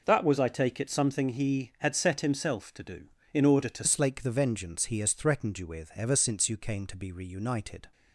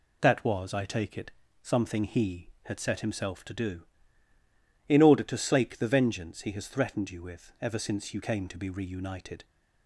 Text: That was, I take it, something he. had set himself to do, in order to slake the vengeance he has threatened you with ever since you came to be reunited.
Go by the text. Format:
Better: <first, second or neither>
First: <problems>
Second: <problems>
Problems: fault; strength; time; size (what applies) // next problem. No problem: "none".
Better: second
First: changes voice at "slake"; from 3.8 s on; 4.0 s long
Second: none